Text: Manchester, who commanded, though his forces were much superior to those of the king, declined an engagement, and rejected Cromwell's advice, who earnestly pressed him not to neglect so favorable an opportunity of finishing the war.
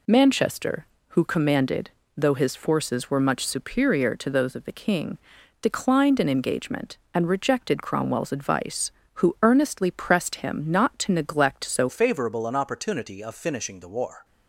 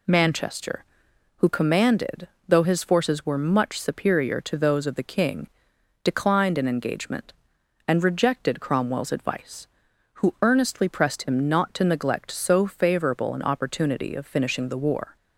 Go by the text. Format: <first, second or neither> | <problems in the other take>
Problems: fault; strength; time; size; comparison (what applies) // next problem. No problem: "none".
second | changes voice at "favorable"; from 11.8 s on; 2.4 s long